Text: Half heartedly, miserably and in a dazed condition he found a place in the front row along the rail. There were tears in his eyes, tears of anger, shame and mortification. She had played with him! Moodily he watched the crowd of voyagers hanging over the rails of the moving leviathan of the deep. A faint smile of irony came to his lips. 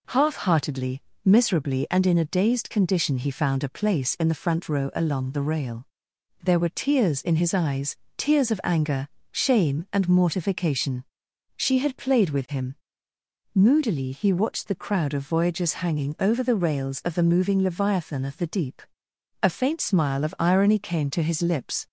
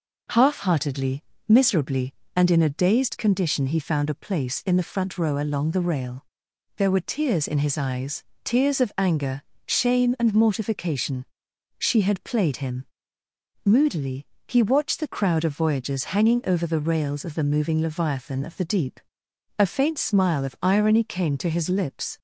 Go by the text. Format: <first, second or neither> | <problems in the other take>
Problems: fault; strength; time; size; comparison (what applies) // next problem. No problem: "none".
first | skips "with"; at 12.5 s // pauses between "Moodily" and "he"; slight; at 14.2 s; 0.22 s long